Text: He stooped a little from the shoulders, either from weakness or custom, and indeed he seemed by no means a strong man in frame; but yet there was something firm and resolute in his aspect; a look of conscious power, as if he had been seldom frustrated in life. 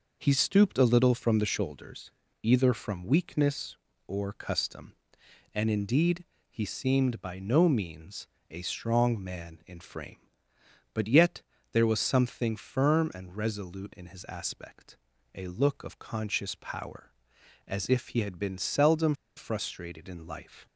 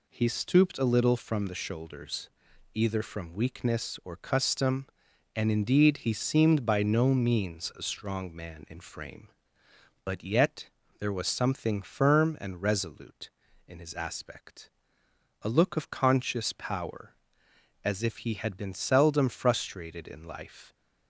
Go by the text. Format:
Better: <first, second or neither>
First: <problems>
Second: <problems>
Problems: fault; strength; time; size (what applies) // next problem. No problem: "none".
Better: second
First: pauses between "indeed" and "he"; slight; at 6.2 s; 0.26 s long // pauses between "means" and "a"; slight; at 8.2 s; 0.24 s long // pauses between "yet" and "there"; slight; at 11.4 s; 0.30 s long // pauses between "seldom" and "frustrated"; slight; at 19.1 s; 0.21 s long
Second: pauses between "yet" and "there"; slight; at 10.6 s; 0.30 s long